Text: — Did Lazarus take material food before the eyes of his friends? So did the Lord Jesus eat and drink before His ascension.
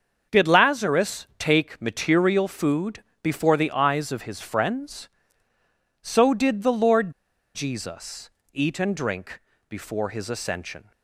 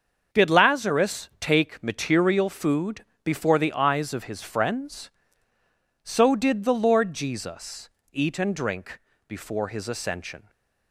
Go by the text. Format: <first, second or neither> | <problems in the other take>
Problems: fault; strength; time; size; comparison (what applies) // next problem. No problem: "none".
second | starts louder than the rest; until 1.4 s; 6.5 dB; also in the second // pauses between "food" and "before"; slight; at 3.0 s; 0.20 s long; slight in the second // pauses between "Lord" and "Jesus"; at 7.1 s; 0.44 s long // pauses between "Jesus" and "eat"; slight; at 8.2 s; 0.24 s long; slight in the second // pauses between "drink" and "before"; slight; at 9.4 s; 0.26 s long; slight in the second